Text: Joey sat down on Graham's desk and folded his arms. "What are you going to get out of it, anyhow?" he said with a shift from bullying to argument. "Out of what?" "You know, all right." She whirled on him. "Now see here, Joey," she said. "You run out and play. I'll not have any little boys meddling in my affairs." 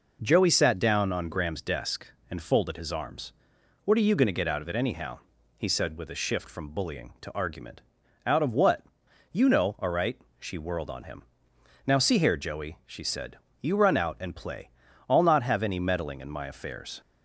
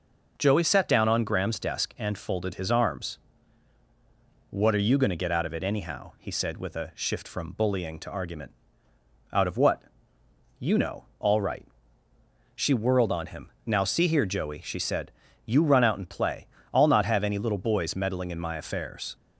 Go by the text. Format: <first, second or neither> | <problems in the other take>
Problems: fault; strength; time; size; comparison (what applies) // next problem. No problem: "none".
second | skips "little boys"; at 15.7 s